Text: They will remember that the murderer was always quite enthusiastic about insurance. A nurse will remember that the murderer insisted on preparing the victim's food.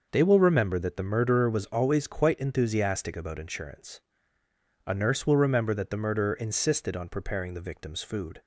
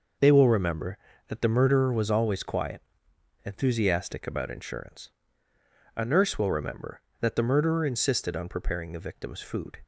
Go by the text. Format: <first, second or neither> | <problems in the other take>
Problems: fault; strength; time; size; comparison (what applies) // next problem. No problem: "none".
first | says "quiet" for "quite"; at 2.4 s